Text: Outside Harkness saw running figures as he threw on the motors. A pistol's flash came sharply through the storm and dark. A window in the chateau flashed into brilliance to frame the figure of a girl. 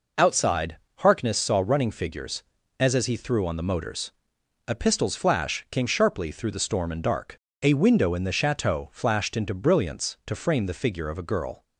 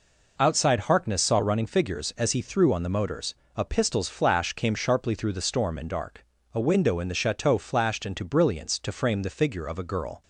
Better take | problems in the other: second | pauses between "Outside" and "Harkness"; slight; at 0.7 s; 0.20 s long // says "as" twice; at 2.9 s

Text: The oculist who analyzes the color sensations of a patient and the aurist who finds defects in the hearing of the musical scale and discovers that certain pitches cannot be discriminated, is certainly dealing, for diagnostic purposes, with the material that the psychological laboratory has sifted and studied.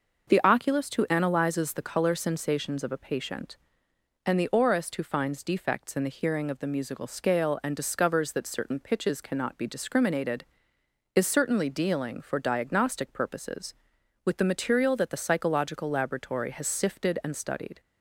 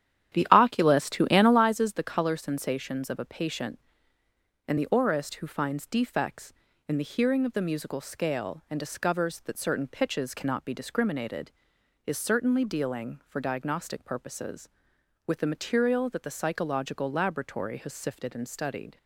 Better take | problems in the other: first | starts louder than the rest; strong; until 1.6 s; 10.5 dB

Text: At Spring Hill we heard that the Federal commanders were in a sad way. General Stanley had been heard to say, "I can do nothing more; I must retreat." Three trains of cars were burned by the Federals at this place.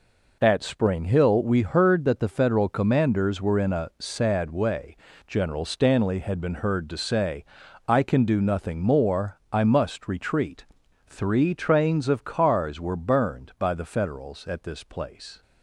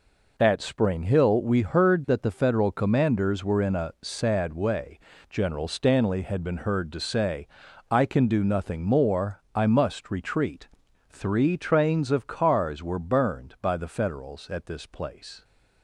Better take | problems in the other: neither | none

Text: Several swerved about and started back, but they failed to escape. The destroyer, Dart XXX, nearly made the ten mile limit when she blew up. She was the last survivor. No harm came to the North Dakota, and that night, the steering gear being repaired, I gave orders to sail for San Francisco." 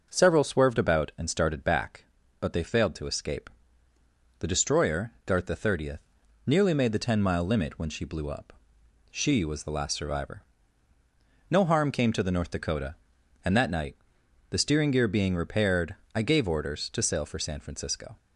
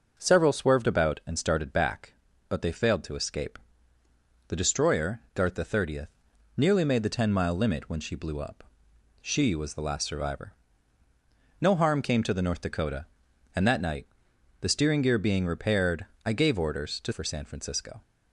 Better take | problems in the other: first | skips "sail"; at 17.1 s

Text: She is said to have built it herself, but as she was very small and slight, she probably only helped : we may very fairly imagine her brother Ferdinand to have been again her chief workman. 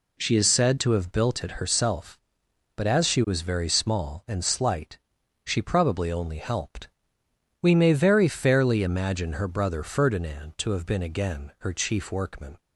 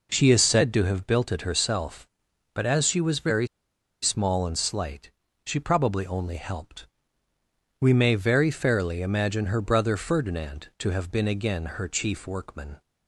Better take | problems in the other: first | pauses between "very" and "small"; noticeable; at 3.4 s; 0.55 s long

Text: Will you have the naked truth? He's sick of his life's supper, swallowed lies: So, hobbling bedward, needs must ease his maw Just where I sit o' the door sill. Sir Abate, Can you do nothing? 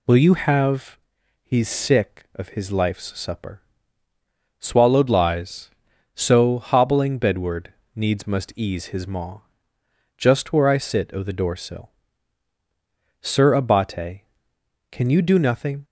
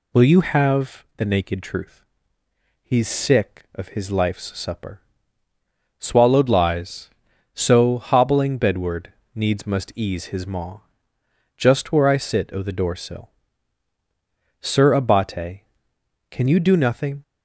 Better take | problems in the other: second | skips "the naked truth"; at 1.2 s // pauses between "maw" and "Just"; noticeable; at 9.4 s; 0.76 s long; noticeable in the second

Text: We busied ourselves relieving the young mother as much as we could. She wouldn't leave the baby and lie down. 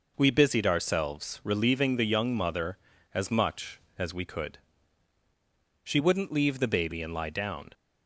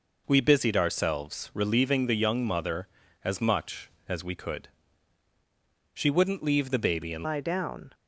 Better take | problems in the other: first | changes voice at "lie"; from 7.2 s on; 0.7 s long

